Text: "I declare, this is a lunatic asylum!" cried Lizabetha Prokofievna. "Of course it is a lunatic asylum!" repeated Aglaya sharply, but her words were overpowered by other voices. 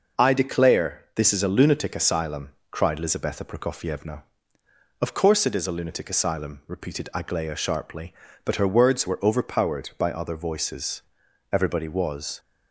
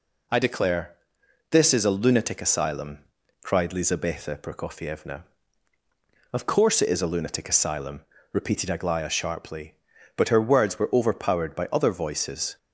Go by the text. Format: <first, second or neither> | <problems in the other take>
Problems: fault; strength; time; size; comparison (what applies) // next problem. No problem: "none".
second | goes on to say "Everybody was"; noticeable; from 11.5 s on; 0.88 s long